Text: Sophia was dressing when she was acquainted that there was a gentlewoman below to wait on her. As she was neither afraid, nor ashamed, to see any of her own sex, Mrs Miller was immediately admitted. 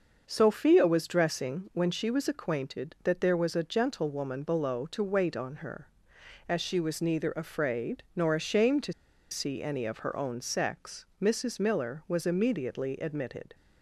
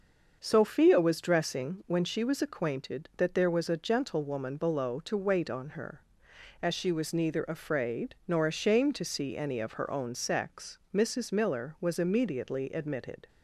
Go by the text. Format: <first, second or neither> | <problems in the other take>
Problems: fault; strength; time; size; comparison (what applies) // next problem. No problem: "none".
second | starts louder than the rest; until 1.2 s; 6 dB; also in the second // pauses between "to" and "see"; at 8.9 s; 0.37 s long